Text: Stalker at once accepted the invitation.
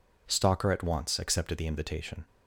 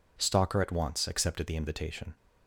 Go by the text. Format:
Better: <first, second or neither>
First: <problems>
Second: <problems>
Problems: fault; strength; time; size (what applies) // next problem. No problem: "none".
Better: neither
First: none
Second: none